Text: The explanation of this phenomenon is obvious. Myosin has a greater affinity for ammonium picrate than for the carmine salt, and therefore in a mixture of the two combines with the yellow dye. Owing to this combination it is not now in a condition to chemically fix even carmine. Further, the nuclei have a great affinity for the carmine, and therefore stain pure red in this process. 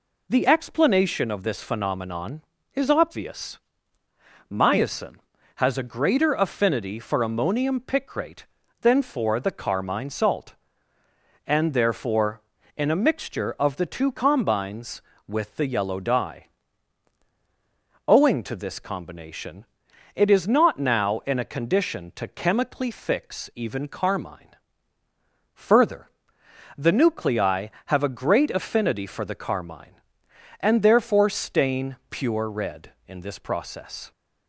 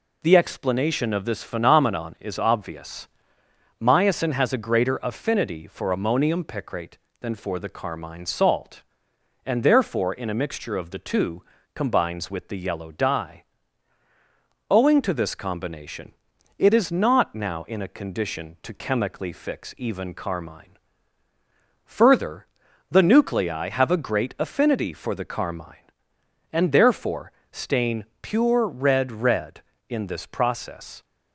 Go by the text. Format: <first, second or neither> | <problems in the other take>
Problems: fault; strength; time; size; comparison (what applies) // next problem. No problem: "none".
first | pauses between "two" and "combines"; slight; at 11.4 s; 0.34 s long // pauses between "combination" and "it"; noticeable; at 16.1 s; 0.46 s long; noticeable in the first // pauses between "therefore" and "stain"; slight; at 27.2 s; 0.22 s long // pauses between "stain" and "pure"; slight; at 28.0 s; 0.16 s long // says "red" twice; at 29.1 s